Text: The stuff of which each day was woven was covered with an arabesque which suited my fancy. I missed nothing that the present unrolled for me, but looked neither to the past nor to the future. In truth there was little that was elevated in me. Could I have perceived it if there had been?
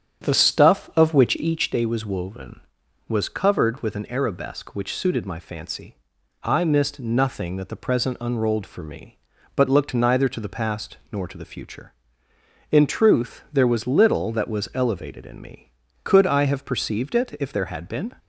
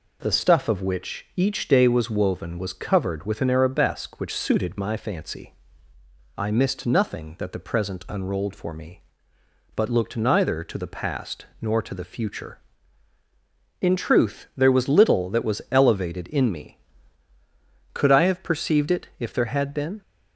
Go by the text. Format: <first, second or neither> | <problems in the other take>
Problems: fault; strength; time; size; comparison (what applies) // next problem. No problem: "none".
second | starts louder than the rest; strong; until 1.7 s; 8.5 dB